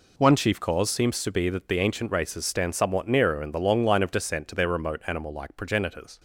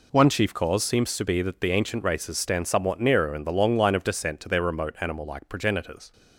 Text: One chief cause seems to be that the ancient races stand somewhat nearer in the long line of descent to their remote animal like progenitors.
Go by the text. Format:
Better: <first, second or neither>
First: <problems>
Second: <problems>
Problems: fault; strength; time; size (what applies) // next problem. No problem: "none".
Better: neither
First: none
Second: none